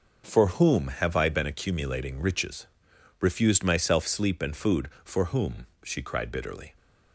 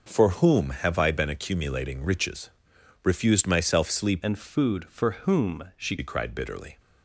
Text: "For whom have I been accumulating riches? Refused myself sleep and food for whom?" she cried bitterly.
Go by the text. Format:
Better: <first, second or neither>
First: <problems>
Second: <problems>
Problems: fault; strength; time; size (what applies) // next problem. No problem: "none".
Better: first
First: none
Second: changes voice from "and" to "she"; from 4.2 to 5.9 s; 1.7 s long